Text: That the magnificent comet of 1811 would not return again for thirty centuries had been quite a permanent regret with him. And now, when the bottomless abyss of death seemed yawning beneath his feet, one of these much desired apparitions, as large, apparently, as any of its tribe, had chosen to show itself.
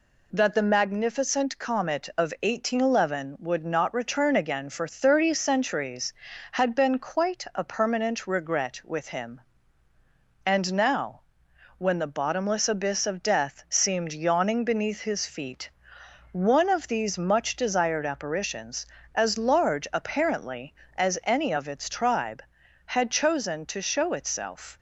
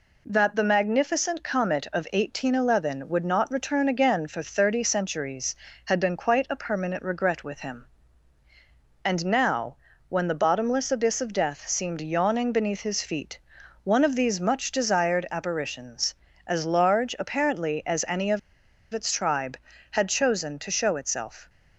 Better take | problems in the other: first | pauses between "of" and "its"; noticeable; at 18.3 s; 0.53 s long

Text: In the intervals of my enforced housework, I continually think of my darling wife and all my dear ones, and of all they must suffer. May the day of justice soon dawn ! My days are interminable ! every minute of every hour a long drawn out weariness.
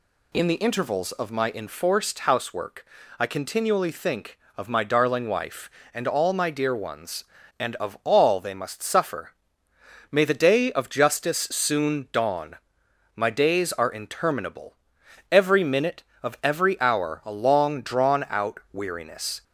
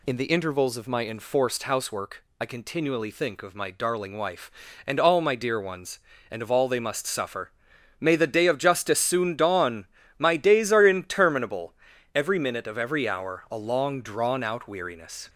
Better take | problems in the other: neither | none

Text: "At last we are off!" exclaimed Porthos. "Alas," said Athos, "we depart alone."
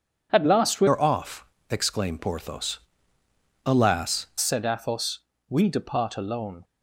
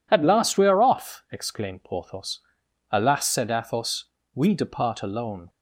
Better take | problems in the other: second | changes voice from "are" to "Alas"; from 0.8 to 4.2 s; 3.4 s long

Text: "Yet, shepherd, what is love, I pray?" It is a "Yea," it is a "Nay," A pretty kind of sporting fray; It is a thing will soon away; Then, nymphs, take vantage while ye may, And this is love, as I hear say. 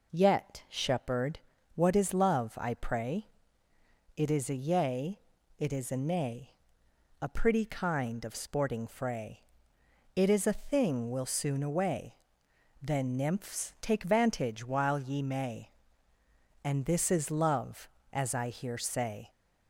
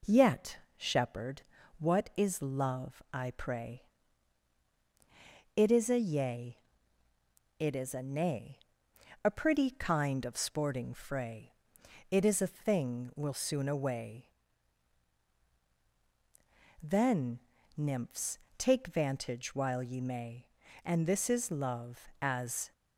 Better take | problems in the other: first | stops before "I hear say"; at 22.7 s

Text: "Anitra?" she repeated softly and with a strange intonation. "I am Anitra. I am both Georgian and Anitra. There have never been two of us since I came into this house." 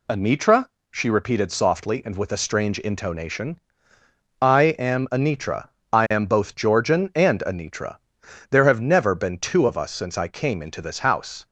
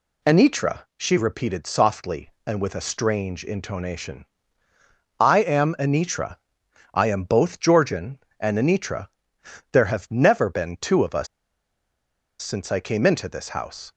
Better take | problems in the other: first | pauses between "us" and "since"; at 11.2 s; 1.1 s long

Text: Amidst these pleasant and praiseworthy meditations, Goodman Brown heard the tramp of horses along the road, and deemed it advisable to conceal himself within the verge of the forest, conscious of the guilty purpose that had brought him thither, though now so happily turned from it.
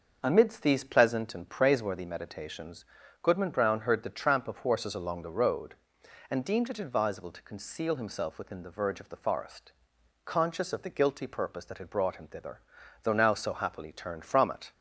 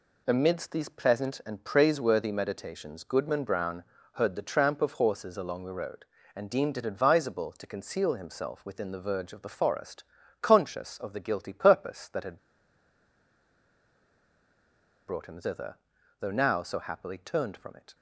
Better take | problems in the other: first | pauses between "Brown" and "heard"; slight; at 3.8 s; 0.30 s long // pauses between "had" and "brought"; strong; at 12.3 s; 2.6 s long

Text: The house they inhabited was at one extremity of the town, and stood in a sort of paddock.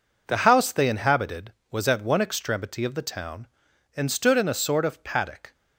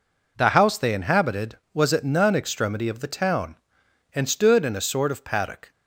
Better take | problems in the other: first | says "none" for "one"; at 2.0 s

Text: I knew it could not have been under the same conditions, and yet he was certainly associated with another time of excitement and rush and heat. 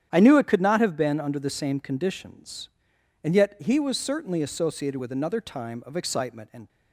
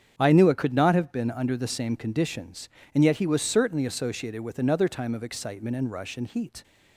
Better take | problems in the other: second | starts louder than the rest; strong; until 1.1 s; 9.5 dB; strong in the second // stops before "rush and heat"; at 6.6 s

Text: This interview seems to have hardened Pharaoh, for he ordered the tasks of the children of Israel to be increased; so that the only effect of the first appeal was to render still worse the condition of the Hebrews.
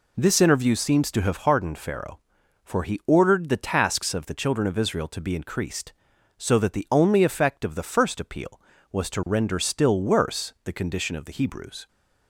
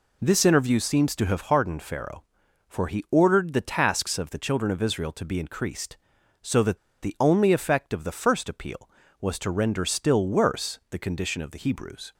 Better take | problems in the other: first | pauses between "that" and "the"; slight; at 6.7 s; 0.25 s long

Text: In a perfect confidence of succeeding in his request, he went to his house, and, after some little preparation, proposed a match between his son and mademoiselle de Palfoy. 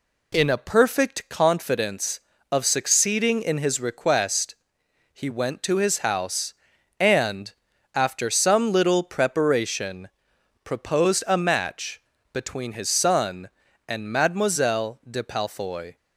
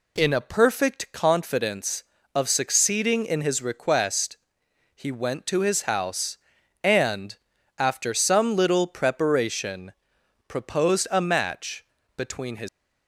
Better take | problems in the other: first | pauses between "match" and "between"; slight; at 11.8 s; 0.32 s long; slight in the first // stops before "son and mademoiselle de Palfoy"; at 12.6 s

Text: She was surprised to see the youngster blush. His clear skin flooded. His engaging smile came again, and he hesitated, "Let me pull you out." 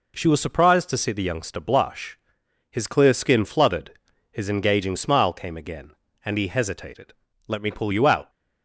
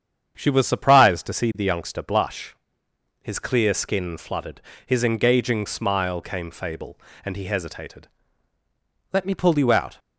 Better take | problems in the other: first | starts louder than the rest; strong; until 1.3 s; 8 dB // says "fable" for "again"; at 6.5 s

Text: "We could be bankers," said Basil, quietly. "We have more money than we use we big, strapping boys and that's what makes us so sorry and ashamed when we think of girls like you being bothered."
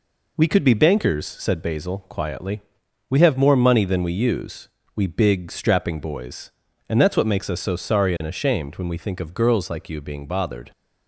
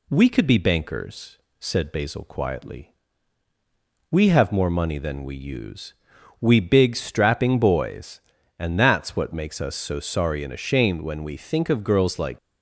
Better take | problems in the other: first | pauses between "use" and "we"; noticeable; at 5.9 s; 0.46 s long; slight in the first // stops before "you being bothered"; at 12.3 s

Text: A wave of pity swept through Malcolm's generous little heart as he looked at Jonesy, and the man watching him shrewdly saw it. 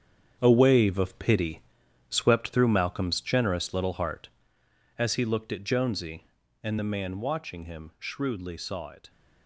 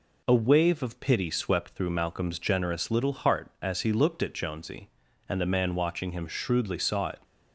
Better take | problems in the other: second | gets quieter; strong; throughout; 9.5 dB // pauses between "pity" and "swept"; noticeable; at 1.6 s; 0.48 s long

